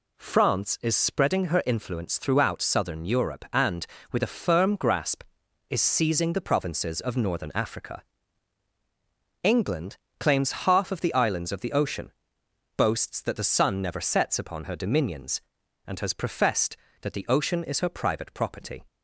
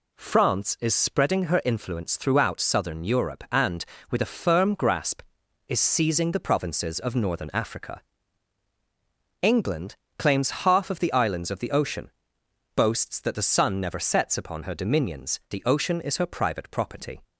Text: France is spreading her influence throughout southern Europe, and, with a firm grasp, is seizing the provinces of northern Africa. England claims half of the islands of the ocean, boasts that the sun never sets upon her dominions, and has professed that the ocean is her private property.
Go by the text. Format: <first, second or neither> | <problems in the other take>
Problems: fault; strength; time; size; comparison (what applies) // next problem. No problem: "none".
first | pauses between "England" and "claims"; slight; at 9.9 s; 0.22 s long; slight in the first // skips "and has professed that"; at 15.4 s